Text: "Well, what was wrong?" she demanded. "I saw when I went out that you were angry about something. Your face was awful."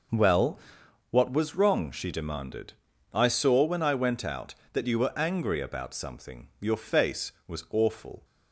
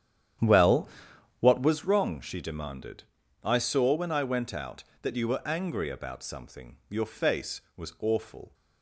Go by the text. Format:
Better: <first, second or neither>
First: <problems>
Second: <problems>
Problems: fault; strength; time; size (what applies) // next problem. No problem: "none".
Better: first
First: none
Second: starts louder than the rest; strong; until 2.0 s; 10 dB